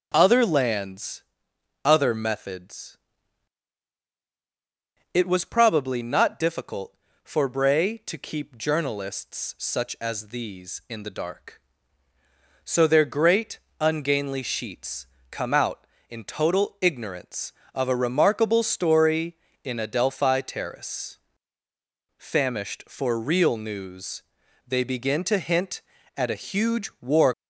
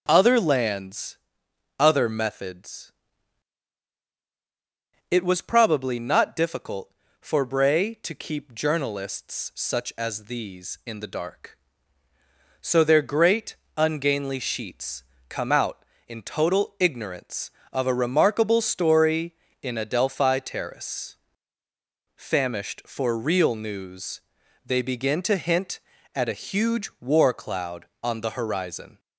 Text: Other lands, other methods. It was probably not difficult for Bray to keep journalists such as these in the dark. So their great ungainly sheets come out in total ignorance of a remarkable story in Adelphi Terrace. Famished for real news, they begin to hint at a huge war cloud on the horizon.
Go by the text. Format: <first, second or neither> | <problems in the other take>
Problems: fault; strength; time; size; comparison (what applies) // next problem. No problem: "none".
second | starts louder than the rest; until 1.1 s; 6.5 dB; also in the second // pauses between "great" and "ungainly"; slight; at 13.5 s; 0.22 s long; slight in the second // pauses between "sheets" and "come"; slight; at 15.0 s; 0.24 s long; slight in the second // stops before "cloud on the horizon"; at 27.3 s